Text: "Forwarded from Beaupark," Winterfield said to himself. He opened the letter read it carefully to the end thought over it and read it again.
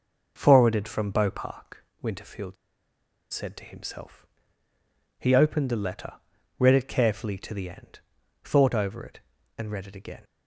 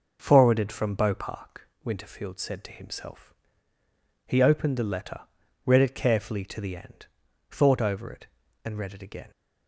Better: second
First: pauses between "Winterfield" and "said"; noticeable; at 2.5 s; 0.77 s long // pauses between "letter" and "read"; at 6.1 s; 0.44 s long // pauses between "end" and "thought"; at 7.9 s; 0.44 s long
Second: pauses between "letter" and "read"; at 5.2 s; 0.43 s long // pauses between "end" and "thought"; at 7.0 s; 0.44 s long

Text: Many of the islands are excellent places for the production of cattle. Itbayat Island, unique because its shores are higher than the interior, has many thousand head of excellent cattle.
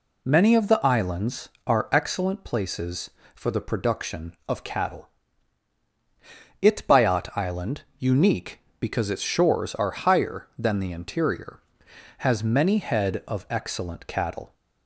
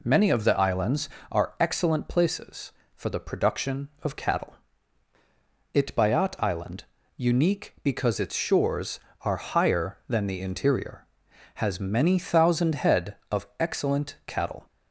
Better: second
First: skips "thousand"; at 12.7 s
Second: none

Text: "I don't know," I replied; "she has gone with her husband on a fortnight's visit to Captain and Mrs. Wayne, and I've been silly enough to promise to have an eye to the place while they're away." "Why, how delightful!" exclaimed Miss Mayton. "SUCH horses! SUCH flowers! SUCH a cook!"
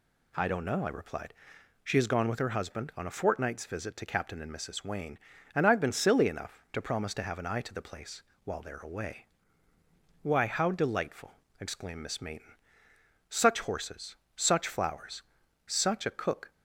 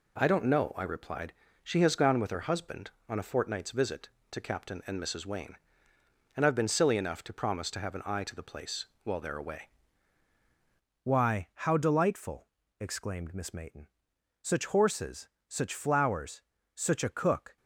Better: first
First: pauses between "place" and "while"; slight; at 8.2 s; 0.22 s long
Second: pauses between "place" and "while"; slight; at 8.8 s; 0.16 s long // changes voice at "Why"; from 11.0 s on; 6.5 s long

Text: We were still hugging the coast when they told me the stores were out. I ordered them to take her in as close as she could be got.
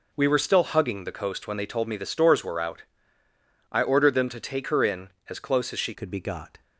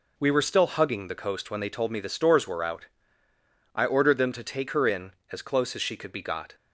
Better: second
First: changes voice at "could"; from 5.9 s on; 0.7 s long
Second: none

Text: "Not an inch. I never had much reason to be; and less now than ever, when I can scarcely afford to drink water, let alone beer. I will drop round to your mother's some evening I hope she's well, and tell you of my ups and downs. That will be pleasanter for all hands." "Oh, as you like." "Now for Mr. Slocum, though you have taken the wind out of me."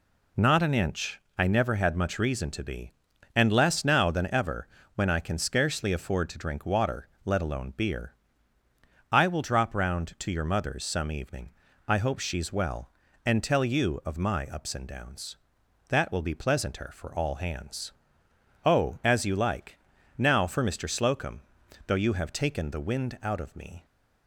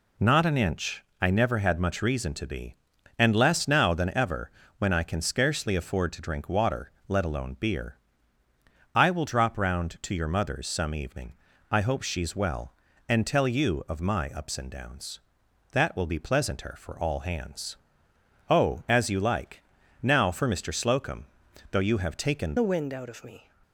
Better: first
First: pauses between "evening" and "I"; slight; at 11.4 s; 0.36 s long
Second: pauses between "evening" and "I"; slight; at 11.3 s; 0.36 s long // changes voice at "the"; from 22.5 s on; 0.9 s long

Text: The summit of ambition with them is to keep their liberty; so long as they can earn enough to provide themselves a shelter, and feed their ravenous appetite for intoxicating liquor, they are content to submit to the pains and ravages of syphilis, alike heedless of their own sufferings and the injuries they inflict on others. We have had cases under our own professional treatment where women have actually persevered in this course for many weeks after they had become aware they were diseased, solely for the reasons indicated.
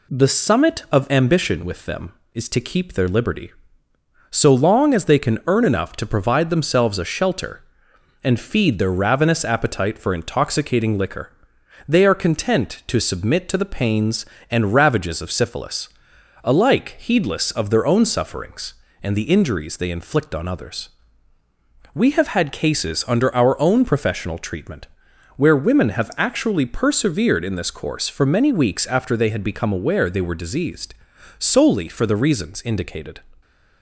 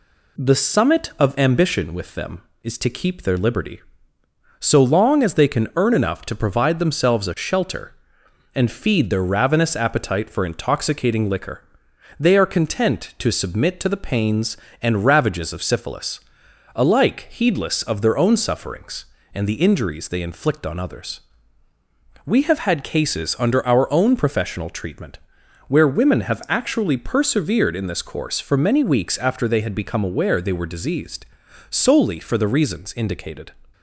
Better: neither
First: pauses between "treatment" and "where"; noticeable; at 24.8 s; 0.50 s long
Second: pauses between "treatment" and "where"; noticeable; at 25.1 s; 0.50 s long

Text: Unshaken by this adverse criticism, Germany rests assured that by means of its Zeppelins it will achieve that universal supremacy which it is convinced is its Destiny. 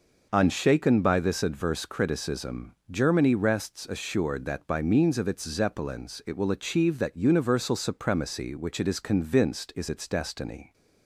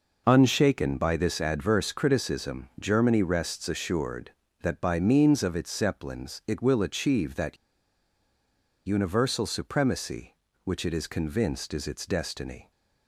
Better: first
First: none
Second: pauses between "that" and "universal"; strong; at 7.5 s; 1.3 s long

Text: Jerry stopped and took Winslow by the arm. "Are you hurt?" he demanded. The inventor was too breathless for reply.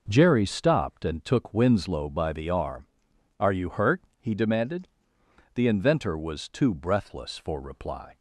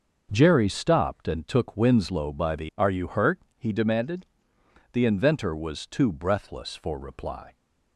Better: first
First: none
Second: starts louder than the rest; noticeable; until 1.3 s; 6 dB // skips "arm"; at 2.7 s

